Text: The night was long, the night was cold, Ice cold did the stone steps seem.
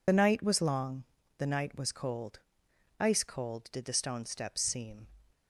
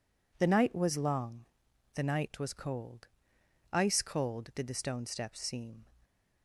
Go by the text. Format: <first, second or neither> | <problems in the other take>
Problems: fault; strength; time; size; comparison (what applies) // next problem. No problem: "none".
second | loses the start of "The"; at 0.0 s; 35 ms